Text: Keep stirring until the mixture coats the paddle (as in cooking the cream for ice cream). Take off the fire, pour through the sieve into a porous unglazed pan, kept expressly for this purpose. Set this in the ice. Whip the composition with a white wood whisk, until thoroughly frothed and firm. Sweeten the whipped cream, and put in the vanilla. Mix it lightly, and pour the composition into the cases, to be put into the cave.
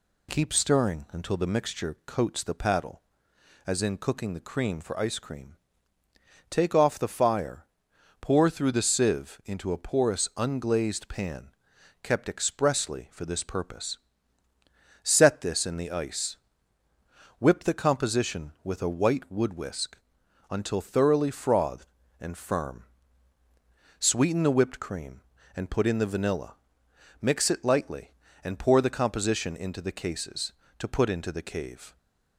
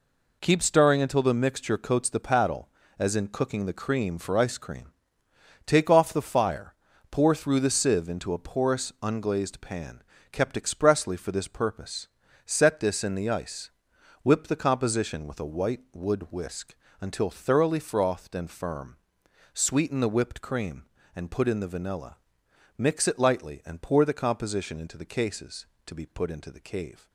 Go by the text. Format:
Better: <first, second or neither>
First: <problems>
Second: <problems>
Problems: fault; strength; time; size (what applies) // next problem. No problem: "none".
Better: second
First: skips "be"; at 30.8 s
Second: none